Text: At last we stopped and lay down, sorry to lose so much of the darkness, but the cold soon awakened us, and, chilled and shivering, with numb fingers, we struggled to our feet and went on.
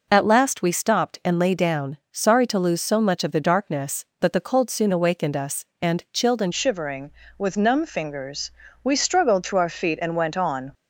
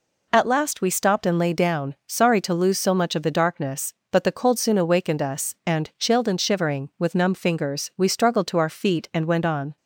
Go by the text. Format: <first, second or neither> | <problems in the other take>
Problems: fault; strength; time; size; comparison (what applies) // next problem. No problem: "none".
second | changes voice at "shivering"; from 6.5 s on; 4.2 s long